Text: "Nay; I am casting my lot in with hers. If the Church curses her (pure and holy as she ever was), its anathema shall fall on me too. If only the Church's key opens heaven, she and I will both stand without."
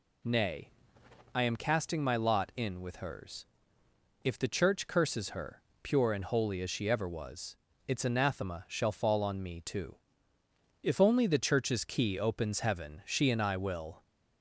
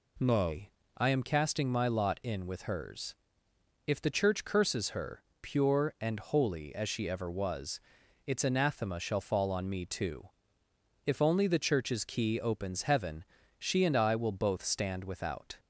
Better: second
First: stops before "both stand without"; at 14.0 s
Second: none

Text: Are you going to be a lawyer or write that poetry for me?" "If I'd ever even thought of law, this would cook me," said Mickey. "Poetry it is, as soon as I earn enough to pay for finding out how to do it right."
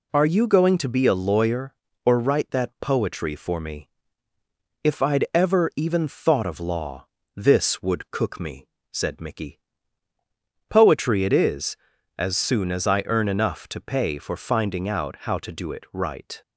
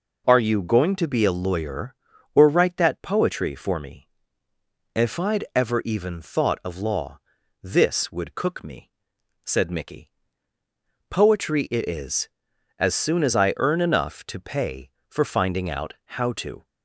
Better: first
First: none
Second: pauses between "out" and "how"; slight; at 15.9 s; 0.24 s long // stops before "do it right"; at 16.6 s

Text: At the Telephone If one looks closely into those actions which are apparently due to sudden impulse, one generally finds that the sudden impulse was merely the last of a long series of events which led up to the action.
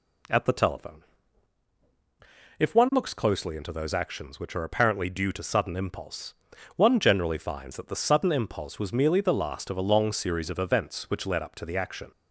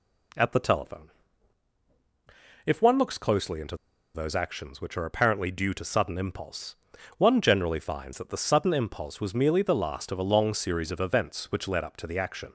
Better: first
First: pauses between "Telephone" and "If"; strong; at 1.0 s; 1.5 s long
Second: pauses between "Telephone" and "If"; strong; at 1.0 s; 1.5 s long // pauses between "into" and "those"; at 3.7 s; 0.39 s long

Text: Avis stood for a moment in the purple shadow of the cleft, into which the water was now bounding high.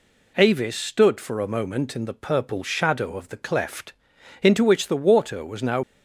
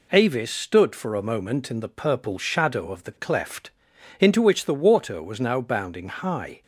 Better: second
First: stops before "bounding high"; at 5.8 s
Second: none

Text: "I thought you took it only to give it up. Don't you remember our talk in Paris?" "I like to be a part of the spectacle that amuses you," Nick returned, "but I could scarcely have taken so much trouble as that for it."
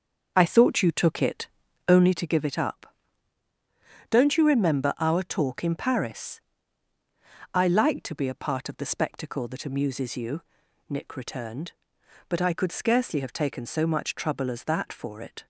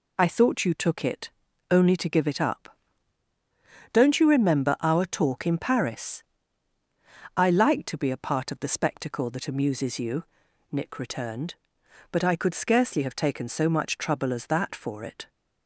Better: second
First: starts louder than the rest; until 2.2 s; 6.5 dB // pauses between "it" and "only"; at 1.4 s; 0.40 s long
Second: pauses between "it" and "only"; at 1.3 s; 0.40 s long

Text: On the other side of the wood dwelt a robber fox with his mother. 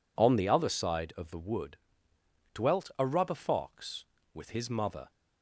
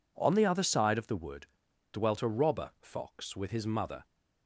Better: second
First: pauses between "wood" and "dwelt"; noticeable; at 1.7 s; 0.78 s long // says "rubber" for "robber"; at 3.0 s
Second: pauses between "wood" and "dwelt"; noticeable; at 1.4 s; 0.46 s long

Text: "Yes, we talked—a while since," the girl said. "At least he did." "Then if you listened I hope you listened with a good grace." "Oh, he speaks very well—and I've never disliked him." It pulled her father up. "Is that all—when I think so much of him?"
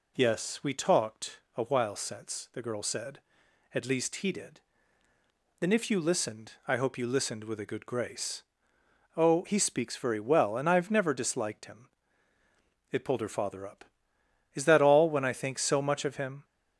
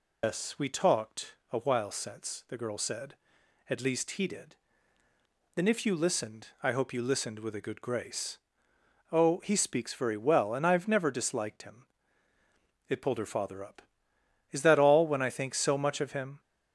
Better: first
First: pauses between "listened" and "I"; slight; at 6.5 s; 0.16 s long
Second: loses the start of "Yes"; at 0.2 s; 120 ms // pauses between "listened" and "I"; slight; at 6.4 s; 0.16 s long

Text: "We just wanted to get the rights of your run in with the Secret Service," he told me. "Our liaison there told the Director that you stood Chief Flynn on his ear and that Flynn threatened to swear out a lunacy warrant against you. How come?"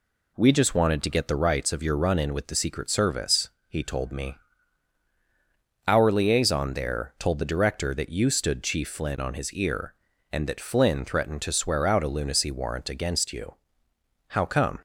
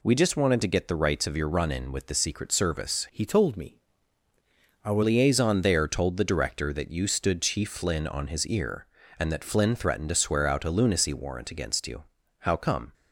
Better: first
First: none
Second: changes voice from "he" to "Our"; from 3.1 to 5.0 s; 1.9 s long

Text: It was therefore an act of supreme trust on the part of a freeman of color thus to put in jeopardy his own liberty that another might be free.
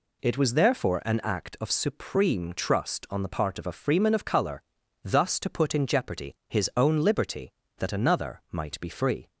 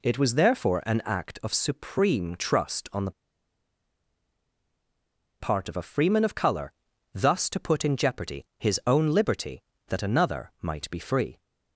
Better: first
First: pauses between "color" and "thus"; at 4.6 s; 0.40 s long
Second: pauses between "the" and "part"; strong; at 3.1 s; 2.2 s long // pauses between "color" and "thus"; at 6.7 s; 0.40 s long

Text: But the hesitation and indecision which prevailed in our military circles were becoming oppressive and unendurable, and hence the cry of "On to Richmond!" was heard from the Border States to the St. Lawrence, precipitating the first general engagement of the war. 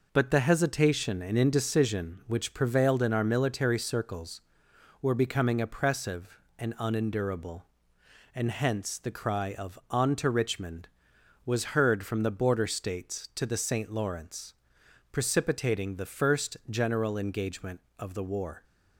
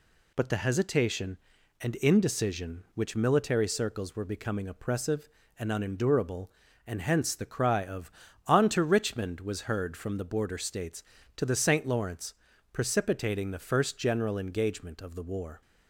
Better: first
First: none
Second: skips "prevailed in our"; at 3.1 s

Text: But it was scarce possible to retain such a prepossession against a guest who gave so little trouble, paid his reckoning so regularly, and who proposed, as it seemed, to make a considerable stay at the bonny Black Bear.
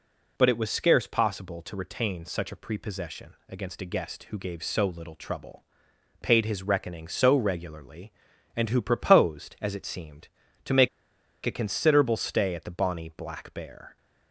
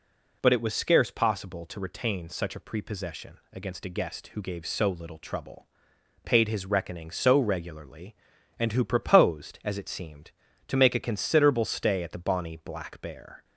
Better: second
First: pauses between "make" and "a"; noticeable; at 10.8 s; 0.57 s long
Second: none

